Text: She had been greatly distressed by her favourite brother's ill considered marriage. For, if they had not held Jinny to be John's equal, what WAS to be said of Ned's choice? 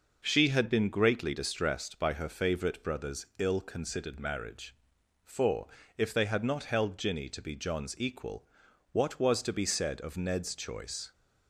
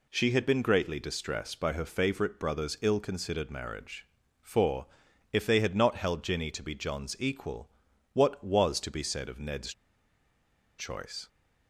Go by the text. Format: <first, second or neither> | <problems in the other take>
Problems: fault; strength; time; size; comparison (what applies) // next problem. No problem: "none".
first | pauses between "Ned's" and "choice"; at 9.7 s; 1.0 s long